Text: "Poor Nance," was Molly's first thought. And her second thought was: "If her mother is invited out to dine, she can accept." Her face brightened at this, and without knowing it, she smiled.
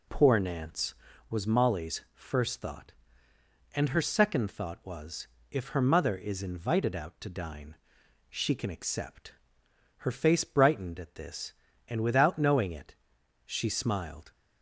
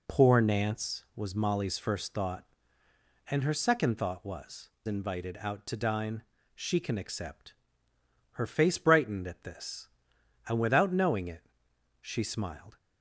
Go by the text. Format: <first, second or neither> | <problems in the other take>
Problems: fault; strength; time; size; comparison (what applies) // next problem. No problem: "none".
first | skips "If her mother is"; at 4.7 s